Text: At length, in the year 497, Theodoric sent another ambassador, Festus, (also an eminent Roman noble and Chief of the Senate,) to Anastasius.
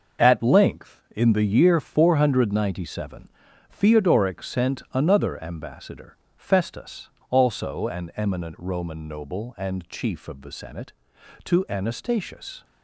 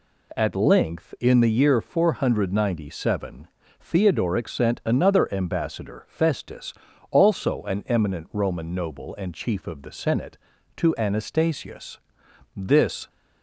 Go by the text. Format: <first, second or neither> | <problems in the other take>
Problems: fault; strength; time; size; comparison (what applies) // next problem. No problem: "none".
first | goes on to say "This"; from 12.5 s on; 0.54 s long